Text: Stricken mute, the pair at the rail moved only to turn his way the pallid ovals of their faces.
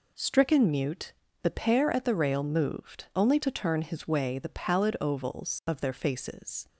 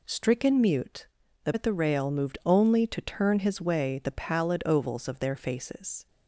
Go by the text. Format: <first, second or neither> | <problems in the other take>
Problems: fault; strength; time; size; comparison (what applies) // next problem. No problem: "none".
first | skips "pair"; at 1.5 s